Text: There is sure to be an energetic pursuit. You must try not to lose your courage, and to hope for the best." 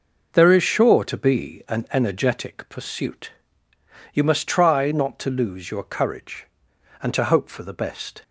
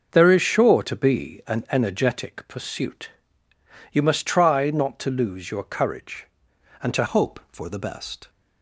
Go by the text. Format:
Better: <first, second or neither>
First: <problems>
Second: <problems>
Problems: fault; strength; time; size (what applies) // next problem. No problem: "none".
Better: first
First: none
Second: starts louder than the rest; until 1.1 s; 6.5 dB // changes voice at "hope"; from 7.0 s on; 1.2 s long